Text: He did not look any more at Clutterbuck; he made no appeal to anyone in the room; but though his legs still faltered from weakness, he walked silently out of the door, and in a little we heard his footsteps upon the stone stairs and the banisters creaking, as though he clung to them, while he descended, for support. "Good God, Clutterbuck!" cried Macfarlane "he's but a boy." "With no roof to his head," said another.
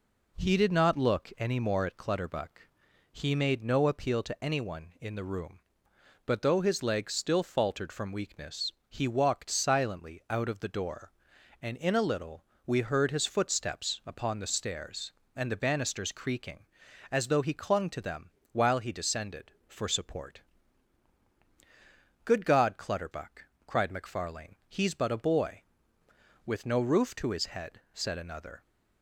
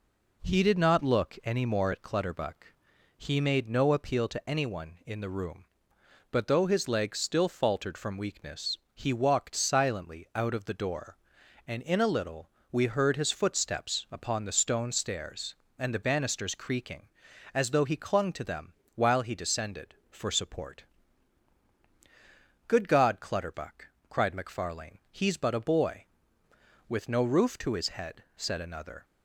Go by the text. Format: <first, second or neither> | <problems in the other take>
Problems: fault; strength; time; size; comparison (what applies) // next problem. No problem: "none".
second | pauses between "little" and "we"; slight; at 12.4 s; 0.24 s long; slight in the second // skips "stone"; at 14.4 s